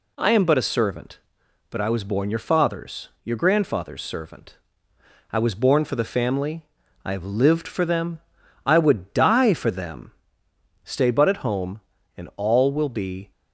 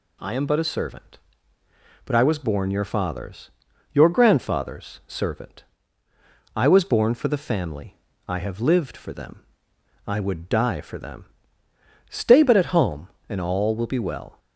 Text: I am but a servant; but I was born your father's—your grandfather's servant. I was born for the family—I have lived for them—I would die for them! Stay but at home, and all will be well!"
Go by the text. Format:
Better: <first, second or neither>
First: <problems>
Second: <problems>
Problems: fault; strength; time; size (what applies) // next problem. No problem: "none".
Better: second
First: stops before "well"; at 13.3 s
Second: none